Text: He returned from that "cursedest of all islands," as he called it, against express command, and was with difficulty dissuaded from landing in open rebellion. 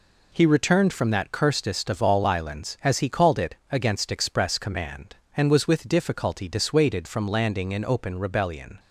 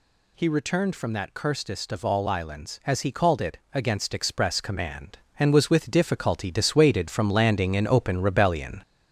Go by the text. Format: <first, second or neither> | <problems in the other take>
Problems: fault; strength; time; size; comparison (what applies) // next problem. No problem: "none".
first | gets louder; noticeable; throughout; 4 dB